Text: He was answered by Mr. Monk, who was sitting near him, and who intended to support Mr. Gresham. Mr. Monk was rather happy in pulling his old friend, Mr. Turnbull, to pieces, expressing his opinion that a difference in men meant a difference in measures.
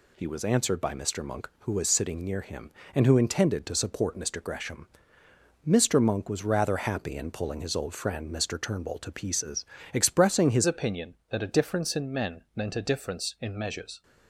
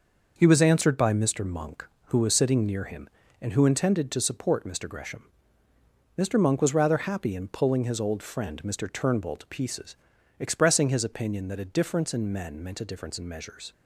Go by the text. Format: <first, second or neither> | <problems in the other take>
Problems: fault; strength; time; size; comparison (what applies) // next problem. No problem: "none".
second | changes voice at "opinion"; from 10.6 s on; 3.4 s long